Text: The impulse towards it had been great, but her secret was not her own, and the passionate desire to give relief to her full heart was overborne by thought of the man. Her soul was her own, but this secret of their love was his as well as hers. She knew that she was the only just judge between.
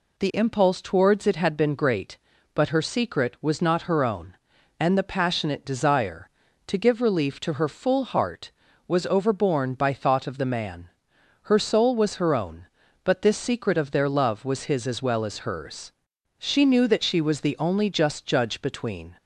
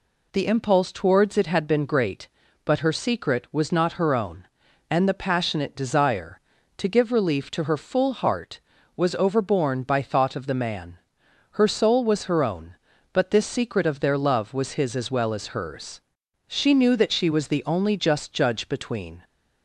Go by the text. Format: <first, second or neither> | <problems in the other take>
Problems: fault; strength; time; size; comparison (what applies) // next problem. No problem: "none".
neither | none